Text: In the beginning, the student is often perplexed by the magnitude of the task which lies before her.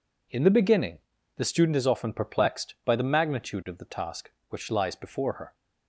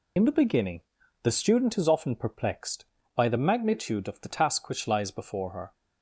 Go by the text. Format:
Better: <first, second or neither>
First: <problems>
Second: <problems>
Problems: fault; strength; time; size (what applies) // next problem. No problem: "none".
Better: first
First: none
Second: loses the start of "In"; at 0.1 s; 25 ms